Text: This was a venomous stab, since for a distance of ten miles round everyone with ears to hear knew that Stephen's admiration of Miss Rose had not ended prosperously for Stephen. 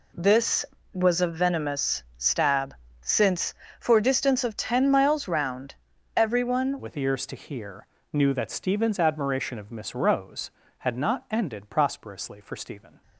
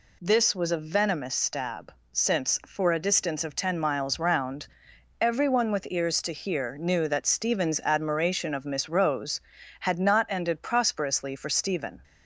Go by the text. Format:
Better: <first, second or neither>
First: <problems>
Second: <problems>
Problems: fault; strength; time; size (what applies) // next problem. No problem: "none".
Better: second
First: pauses between "round" and "everyone"; at 5.7 s; 0.44 s long // changes voice at "with"; from 6.7 s on; 6.3 s long // pauses between "hear" and "knew"; slight; at 7.8 s; 0.26 s long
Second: pauses between "round" and "everyone"; noticeable; at 4.6 s; 0.52 s long